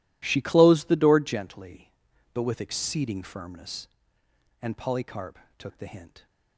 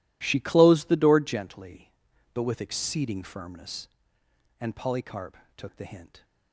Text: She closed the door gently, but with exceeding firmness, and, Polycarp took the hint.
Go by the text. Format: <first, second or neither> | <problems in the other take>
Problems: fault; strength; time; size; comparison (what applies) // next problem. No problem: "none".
neither | pauses between "Polycarp" and "took"; slight; the same in both